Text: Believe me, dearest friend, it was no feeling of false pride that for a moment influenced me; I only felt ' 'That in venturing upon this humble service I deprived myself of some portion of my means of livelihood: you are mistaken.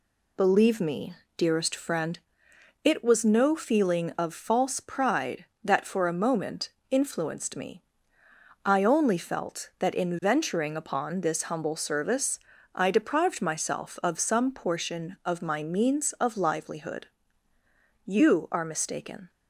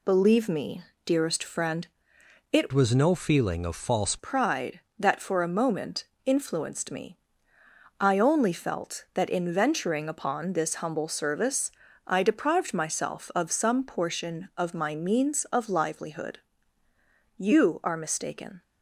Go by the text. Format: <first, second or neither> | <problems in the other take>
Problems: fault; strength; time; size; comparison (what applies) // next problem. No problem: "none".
first | changes voice from "was" to "false"; from 2.7 to 4.1 s; 1.4 s long // pauses between "moment" and "influenced"; slight; at 6.0 s; 0.20 s long; slight in the first // pauses between "service" and "I"; slight; at 11.7 s; 0.34 s long; slight in the first